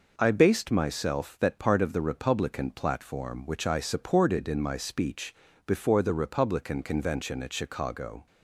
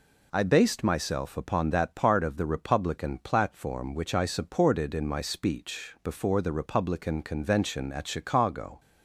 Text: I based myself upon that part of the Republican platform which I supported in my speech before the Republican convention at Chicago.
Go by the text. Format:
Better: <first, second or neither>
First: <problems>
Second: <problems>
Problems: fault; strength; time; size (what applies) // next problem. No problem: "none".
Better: second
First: skips "upon"; at 1.3 s // pauses between "speech" and "before"; slight; at 5.3 s; 0.32 s long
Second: none